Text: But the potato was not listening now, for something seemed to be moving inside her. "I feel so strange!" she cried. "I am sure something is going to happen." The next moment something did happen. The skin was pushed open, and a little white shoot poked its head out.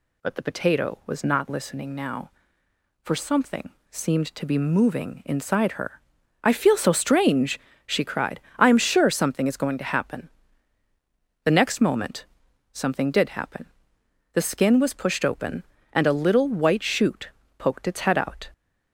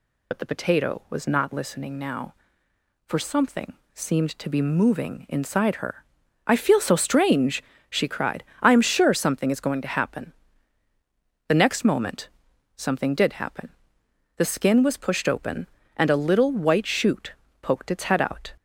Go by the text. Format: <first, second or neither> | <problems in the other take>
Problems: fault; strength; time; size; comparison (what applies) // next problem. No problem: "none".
first | loses the start of "But"; at 0.3 s; 60 ms // pauses between "something" and "seemed"; slight; at 3.7 s; 0.20 s long; slight in the first // pauses between "moment" and "something"; noticeable; at 12.2 s; 0.46 s long; noticeable in the first // pauses between "shoot" and "poked"; slight; at 17.3 s; 0.28 s long; slight in the first